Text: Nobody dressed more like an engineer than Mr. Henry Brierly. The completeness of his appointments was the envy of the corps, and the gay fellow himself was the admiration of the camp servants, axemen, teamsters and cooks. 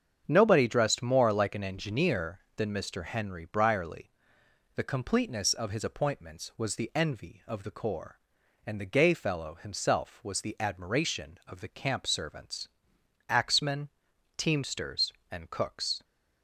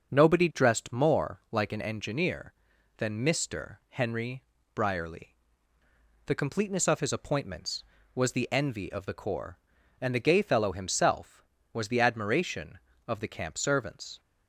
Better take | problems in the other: first | starts louder than the rest; until 1.1 s; 6.5 dB; strong in the first // pauses between "Henry" and "Brierly"; slight; at 4.4 s; 0.30 s long // stops before "axemen teamsters and cooks"; at 14.1 s

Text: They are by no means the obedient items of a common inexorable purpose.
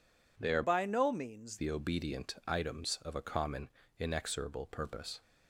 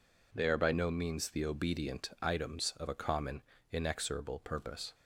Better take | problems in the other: second | changes voice from "by" to "means"; from 0.6 to 1.5 s; 0.9 s long // pauses between "common" and "inexorable"; slight; at 3.6 s; 0.30 s long; slight in the second

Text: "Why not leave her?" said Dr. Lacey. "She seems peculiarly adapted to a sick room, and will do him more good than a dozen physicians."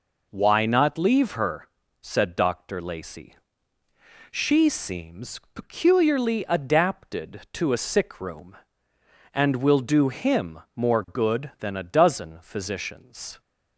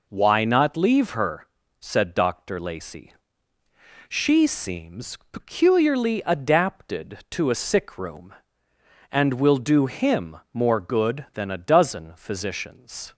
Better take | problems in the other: neither | pauses between "him" and "more"; slight; the same in both

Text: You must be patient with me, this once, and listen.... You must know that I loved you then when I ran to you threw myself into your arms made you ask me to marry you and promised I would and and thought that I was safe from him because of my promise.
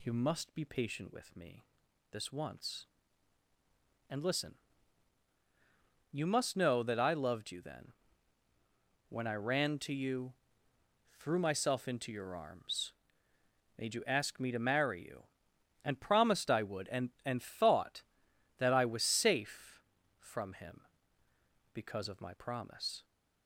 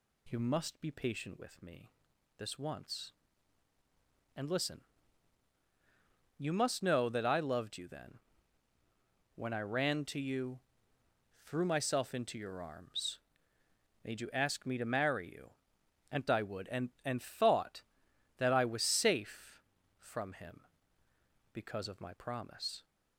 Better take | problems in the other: first | pauses between "then" and "when"; at 8.1 s; 1.1 s long; also in the first // pauses between "you" and "threw"; noticeable; at 10.5 s; 0.84 s long; noticeable in the first // pauses between "arms" and "made"; noticeable; at 13.1 s; 0.88 s long; noticeable in the first // skips "promised"; at 16.2 s

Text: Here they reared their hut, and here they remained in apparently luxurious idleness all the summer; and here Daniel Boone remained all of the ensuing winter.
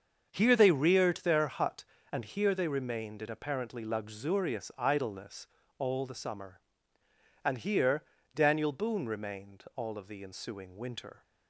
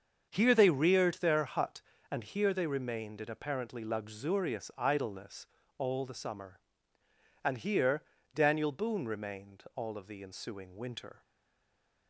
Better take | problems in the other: first | starts louder than the rest; until 1.3 s; 7 dB; also in the first // pauses between "idleness" and "all"; slight; at 5.4 s; 0.32 s long; slight in the first // pauses between "here" and "Daniel"; slight; at 8.0 s; 0.32 s long; slight in the first // stays silent after the last word; slight; from 11.2 s on; 0.8 s long

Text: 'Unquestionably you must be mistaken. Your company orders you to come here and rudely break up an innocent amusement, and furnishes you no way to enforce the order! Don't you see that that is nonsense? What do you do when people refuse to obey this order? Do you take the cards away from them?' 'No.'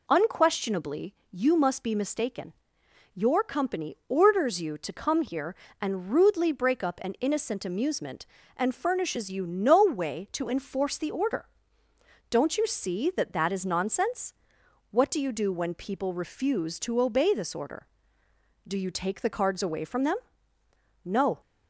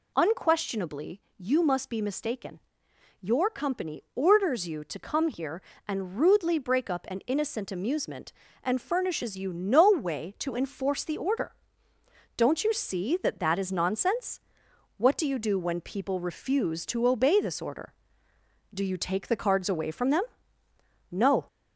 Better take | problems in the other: first | gets louder; throughout; 3.5 dB // pauses between "Unquestionably" and "you"; slight; at 1.2 s; 0.16 s long; slight in the first

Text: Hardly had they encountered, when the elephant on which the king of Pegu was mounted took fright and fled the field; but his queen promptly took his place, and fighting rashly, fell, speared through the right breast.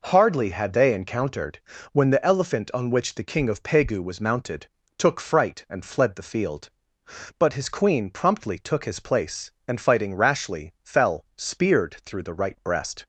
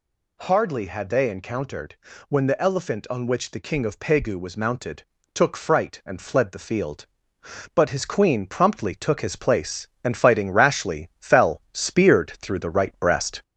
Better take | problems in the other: first | gets louder; slight; throughout; 2.5 dB // pauses between "mounted" and "took"; slight; at 5.0 s; 0.32 s long; slight in the first

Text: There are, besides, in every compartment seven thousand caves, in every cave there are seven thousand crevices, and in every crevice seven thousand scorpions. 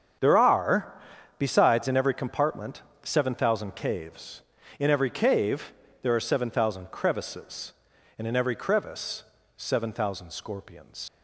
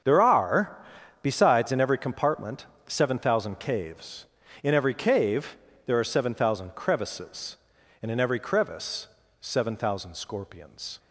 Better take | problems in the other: second | starts louder than the rest; until 1.6 s; 7 dB; also in the second // pauses between "compartment" and "seven"; slight; at 2.8 s; 0.20 s long; slight in the second // pauses between "cave" and "there"; slight; at 5.7 s; 0.30 s long; slight in the second // pauses between "crevice" and "seven"; slight; at 9.2 s; 0.34 s long; slight in the second // leaves "scorpions" unfinished; at 11.0 s; 65 ms

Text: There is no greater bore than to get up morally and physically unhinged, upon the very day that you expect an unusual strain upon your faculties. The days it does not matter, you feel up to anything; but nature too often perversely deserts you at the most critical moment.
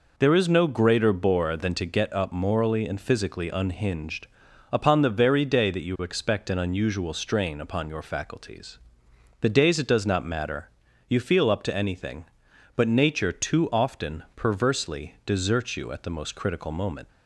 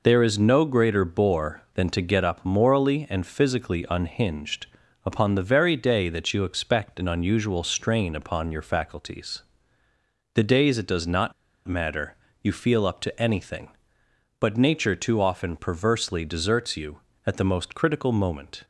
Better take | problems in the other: first | pauses between "not" and "matter"; slight; at 11.3 s; 0.35 s long

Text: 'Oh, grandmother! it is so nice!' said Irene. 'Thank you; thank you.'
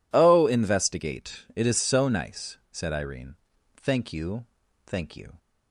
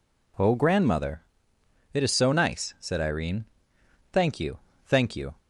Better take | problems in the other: second | says "investigate" for "grandmother"; at 0.4 s

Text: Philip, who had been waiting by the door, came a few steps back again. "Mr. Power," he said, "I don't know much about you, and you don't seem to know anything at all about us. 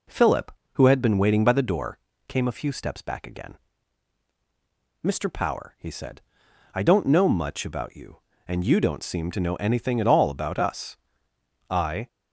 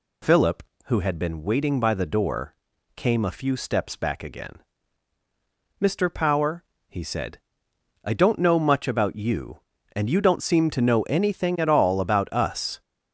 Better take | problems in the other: second | goes on to say "I"; slight; from 11.6 s on; 0.38 s long

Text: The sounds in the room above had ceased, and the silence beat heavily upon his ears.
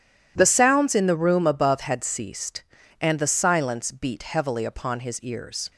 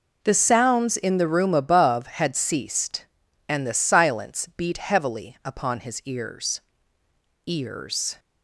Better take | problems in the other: first | says "ears" twice; at 7.4 s

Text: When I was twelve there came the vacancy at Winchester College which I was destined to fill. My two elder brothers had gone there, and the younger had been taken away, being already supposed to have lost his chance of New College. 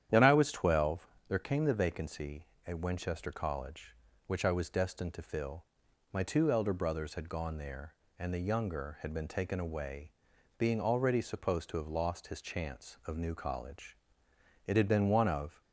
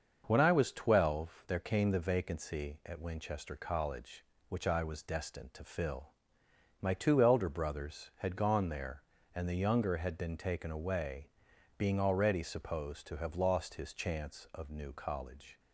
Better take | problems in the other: second | starts louder than the rest; strong; until 1.3 s; 10 dB; also in the second // pauses between "twelve" and "there"; slight; at 1.0 s; 0.22 s long // goes on to say "It had been one of"; noticeable; from 14.6 s on; 0.94 s long

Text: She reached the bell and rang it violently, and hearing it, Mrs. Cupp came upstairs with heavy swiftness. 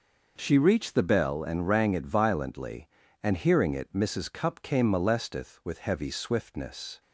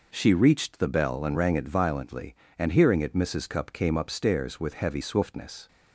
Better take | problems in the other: second | says "molesteth" for "upstairs"; at 4.8 s

